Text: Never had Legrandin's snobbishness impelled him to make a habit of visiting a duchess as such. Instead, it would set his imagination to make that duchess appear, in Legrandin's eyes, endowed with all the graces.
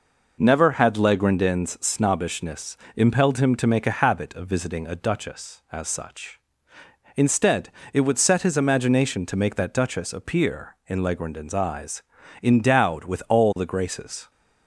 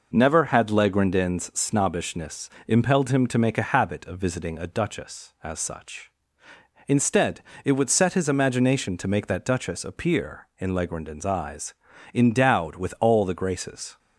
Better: neither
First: pauses between "snobbishness" and "impelled"; slight; at 2.7 s; 0.18 s long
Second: pauses between "snobbishness" and "impelled"; slight; at 2.5 s; 0.16 s long

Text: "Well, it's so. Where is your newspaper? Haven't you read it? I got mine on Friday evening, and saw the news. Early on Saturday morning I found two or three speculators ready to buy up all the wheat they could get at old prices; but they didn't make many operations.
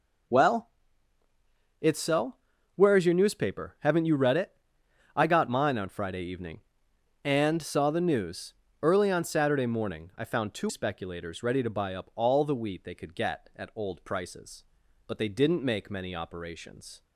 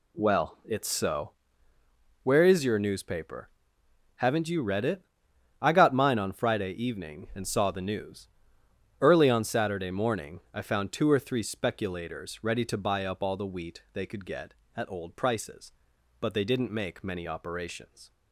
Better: second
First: skips "or three"; at 10.6 s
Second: none

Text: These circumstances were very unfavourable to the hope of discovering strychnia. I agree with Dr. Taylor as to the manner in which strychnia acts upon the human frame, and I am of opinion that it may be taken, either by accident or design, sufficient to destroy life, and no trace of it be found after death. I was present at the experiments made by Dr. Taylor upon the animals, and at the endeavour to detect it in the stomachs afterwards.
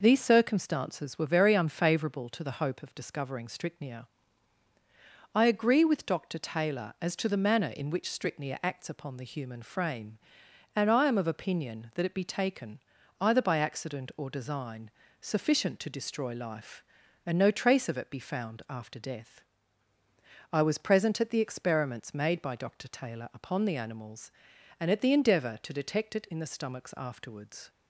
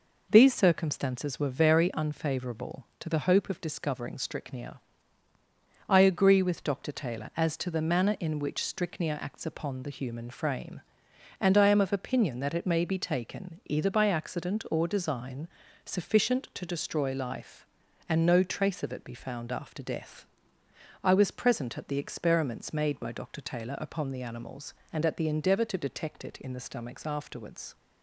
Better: second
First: skips "may"; at 12.1 s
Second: none

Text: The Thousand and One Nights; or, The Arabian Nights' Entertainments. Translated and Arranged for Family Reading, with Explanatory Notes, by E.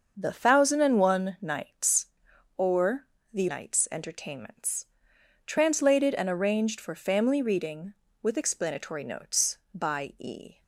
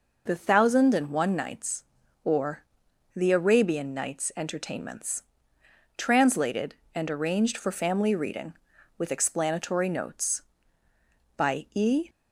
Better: second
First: starts louder than the rest; until 1.1 s; 6.5 dB // skips "Arabian"; at 3.4 s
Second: none

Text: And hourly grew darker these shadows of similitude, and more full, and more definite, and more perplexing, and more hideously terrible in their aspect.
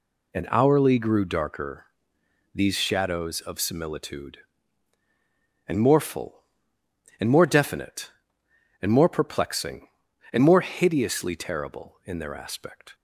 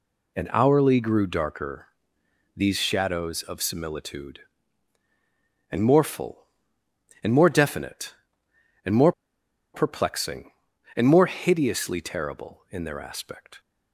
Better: first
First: pauses between "darker" and "these"; noticeable; at 1.8 s; 0.68 s long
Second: pauses between "darker" and "these"; noticeable; at 1.8 s; 0.68 s long // pauses between "more" and "perplexing"; noticeable; at 9.1 s; 0.61 s long

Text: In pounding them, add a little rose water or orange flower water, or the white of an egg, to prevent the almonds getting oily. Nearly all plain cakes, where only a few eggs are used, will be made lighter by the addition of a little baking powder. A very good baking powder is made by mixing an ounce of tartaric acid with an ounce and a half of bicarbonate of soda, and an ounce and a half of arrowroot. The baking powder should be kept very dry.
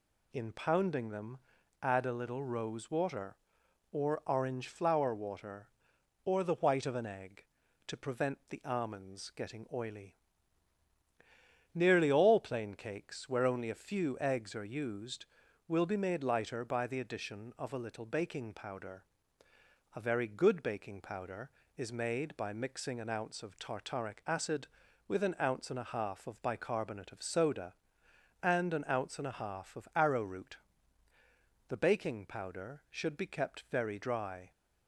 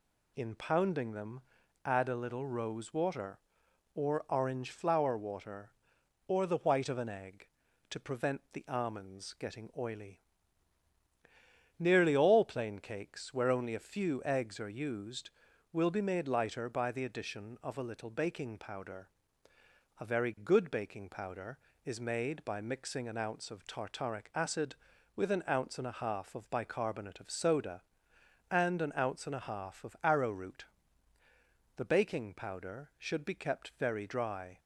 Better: neither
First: none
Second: none

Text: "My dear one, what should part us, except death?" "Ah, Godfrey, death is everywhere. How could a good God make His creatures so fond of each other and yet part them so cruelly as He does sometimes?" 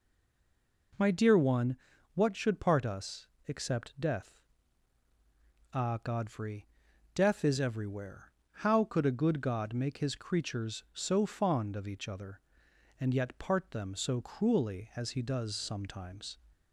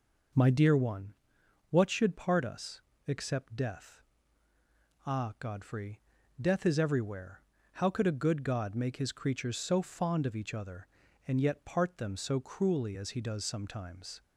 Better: second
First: stays silent before the first word; slight; until 0.9 s; 0.9 s long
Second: none

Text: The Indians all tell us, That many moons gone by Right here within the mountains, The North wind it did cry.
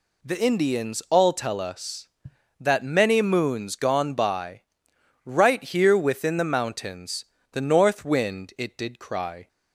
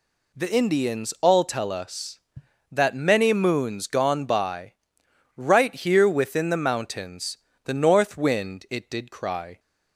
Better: neither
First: pauses between "by" and "Right"; noticeable; at 4.6 s; 0.64 s long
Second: pauses between "by" and "Right"; noticeable; at 4.7 s; 0.64 s long

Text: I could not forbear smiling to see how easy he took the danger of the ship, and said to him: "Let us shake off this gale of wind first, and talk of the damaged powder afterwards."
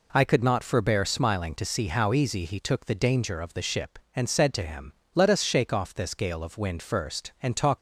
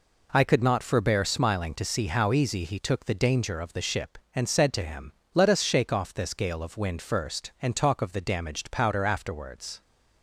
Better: second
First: stops before "of the damaged powder afterwards"; at 7.7 s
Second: none

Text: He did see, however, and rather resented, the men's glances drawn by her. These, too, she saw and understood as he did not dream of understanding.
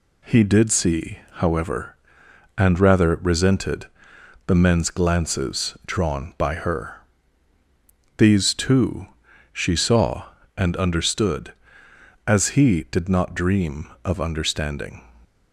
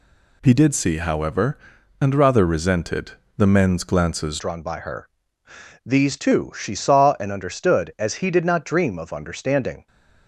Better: first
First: none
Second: changes voice at "drawn"; from 4.3 s on; 5.5 s long

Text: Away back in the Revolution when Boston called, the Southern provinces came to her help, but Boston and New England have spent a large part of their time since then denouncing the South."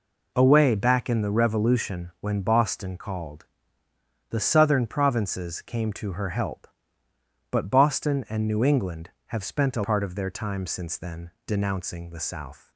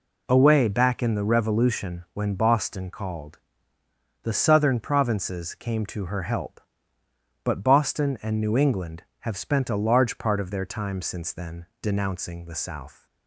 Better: second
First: skips "large"; at 9.8 s // pauses between "then" and "denouncing"; slight; at 11.3 s; 0.16 s long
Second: pauses between "then" and "denouncing"; slight; at 11.6 s; 0.16 s long

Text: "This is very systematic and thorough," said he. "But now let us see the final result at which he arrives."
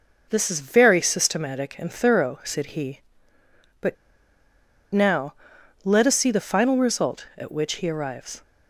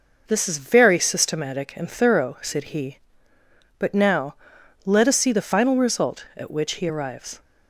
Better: second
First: pauses between "But" and "now"; noticeable; at 3.9 s; 0.97 s long // pauses between "now" and "let"; noticeable; at 5.3 s; 0.50 s long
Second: pauses between "now" and "let"; noticeable; at 4.3 s; 0.50 s long

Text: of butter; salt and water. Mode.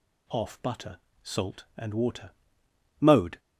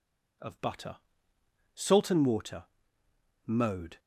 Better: second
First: says "off" for "of"; at 0.2 s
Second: none

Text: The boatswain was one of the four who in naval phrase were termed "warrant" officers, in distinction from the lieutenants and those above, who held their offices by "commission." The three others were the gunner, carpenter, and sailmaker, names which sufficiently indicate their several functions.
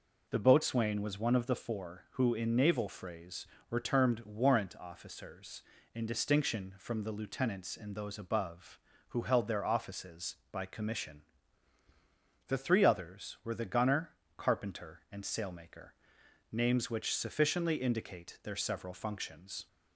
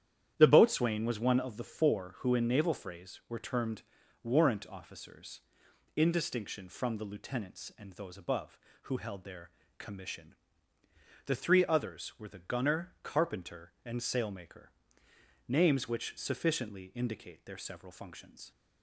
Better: first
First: none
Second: starts louder than the rest; strong; until 1.3 s; 10 dB // pauses between "termed" and "warrant"; at 3.8 s; 0.38 s long // skips "offices by"; at 9.6 s

